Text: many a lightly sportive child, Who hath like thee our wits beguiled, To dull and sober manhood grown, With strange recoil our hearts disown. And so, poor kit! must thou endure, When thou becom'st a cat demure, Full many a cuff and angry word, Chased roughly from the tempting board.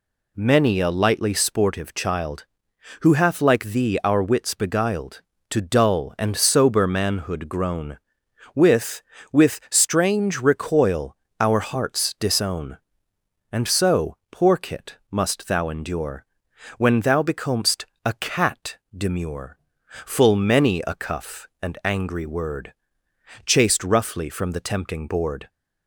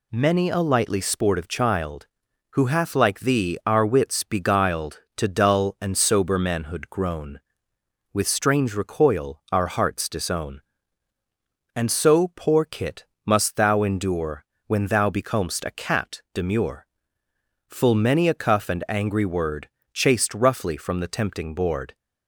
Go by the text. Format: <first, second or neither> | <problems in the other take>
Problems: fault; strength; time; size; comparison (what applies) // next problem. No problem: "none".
second | says "With" twice; at 9.3 s // pauses between "recoil" and "our"; slight; at 11.1 s; 0.24 s long // pauses between "becom'st" and "a"; slight; at 17.8 s; 0.18 s long // pauses between "cat" and "demure"; slight; at 18.7 s; 0.18 s long